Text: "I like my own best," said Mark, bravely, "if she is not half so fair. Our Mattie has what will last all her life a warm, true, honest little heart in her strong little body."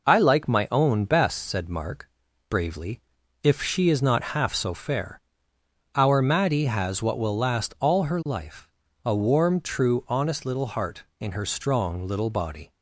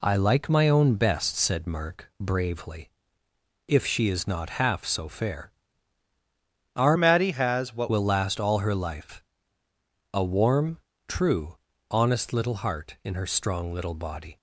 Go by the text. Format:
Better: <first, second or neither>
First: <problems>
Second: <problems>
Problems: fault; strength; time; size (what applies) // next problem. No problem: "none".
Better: first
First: pauses between "life" and "a"; slight; at 8.6 s; 0.36 s long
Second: changes voice from "Mattie" to "what"; from 6.9 to 7.8 s; 0.9 s long // pauses between "life" and "a"; noticeable; at 9.2 s; 0.92 s long